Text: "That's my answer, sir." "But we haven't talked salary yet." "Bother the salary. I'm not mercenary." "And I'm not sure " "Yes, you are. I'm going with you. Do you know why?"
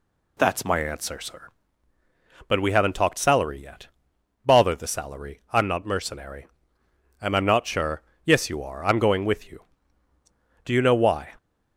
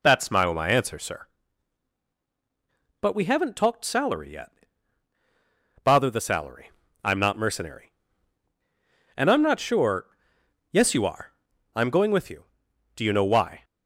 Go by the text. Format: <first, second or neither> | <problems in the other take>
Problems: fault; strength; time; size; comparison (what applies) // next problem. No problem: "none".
first | says "my" twice; at 0.5 s